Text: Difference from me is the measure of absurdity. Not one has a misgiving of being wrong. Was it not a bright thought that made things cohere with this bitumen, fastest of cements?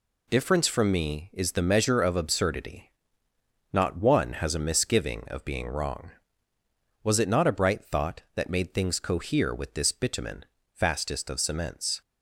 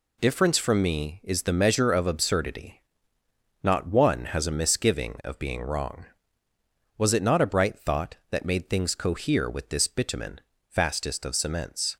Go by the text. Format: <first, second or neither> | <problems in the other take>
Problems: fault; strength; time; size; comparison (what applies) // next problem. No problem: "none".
neither | none